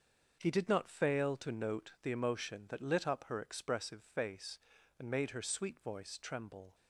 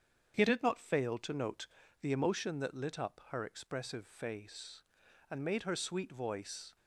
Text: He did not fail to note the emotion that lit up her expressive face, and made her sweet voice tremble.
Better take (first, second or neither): first